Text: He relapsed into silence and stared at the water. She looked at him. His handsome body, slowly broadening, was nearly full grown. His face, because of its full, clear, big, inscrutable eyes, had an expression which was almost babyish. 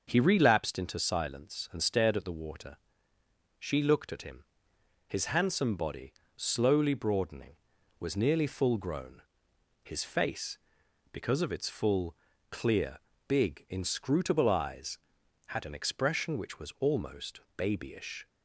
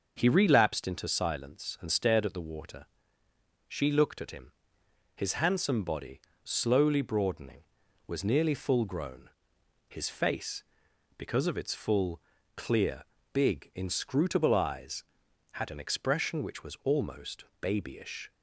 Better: neither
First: starts louder than the rest; until 1.0 s; 6.5 dB // pauses between "almost" and "babyish"; slight; at 17.3 s; 0.16 s long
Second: starts louder than the rest; until 1.1 s; 6.5 dB // pauses between "almost" and "babyish"; slight; at 17.4 s; 0.16 s long

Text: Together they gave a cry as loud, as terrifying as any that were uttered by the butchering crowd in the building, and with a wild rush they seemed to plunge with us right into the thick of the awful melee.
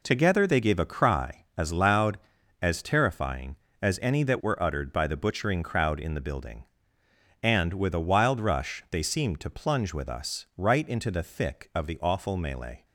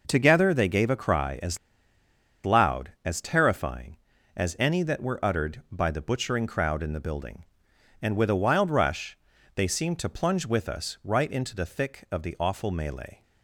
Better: first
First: none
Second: pauses between "as" and "loud"; noticeable; at 1.5 s; 0.86 s long // pauses between "rush" and "they"; at 9.1 s; 0.40 s long

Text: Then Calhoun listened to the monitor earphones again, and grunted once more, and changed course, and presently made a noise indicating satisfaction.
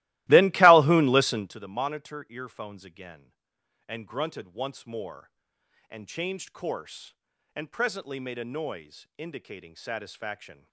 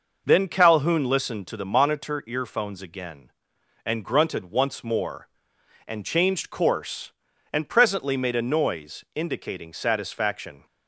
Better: second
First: starts louder than the rest; strong; until 1.6 s; 17.5 dB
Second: none

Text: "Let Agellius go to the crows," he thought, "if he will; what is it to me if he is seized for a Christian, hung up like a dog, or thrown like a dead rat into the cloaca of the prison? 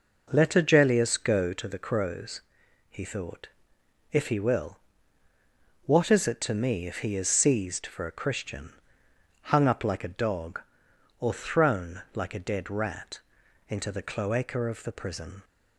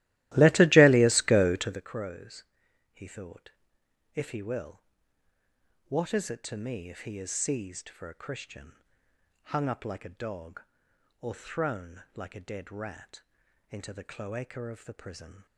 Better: first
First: pauses between "rat" and "into"; noticeable; at 13.1 s; 0.50 s long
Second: starts louder than the rest; strong; until 1.9 s; 16 dB // pauses between "rat" and "into"; noticeable; at 13.2 s; 0.50 s long

